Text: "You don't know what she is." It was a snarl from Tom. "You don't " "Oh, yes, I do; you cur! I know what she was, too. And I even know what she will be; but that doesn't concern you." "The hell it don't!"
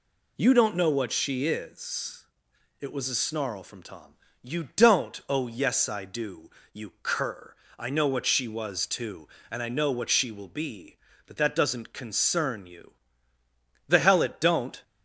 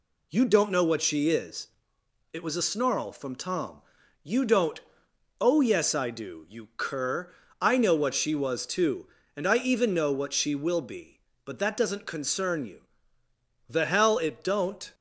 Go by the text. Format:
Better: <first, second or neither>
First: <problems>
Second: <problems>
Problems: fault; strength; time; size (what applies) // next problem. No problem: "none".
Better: second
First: skips "even"; at 9.6 s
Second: none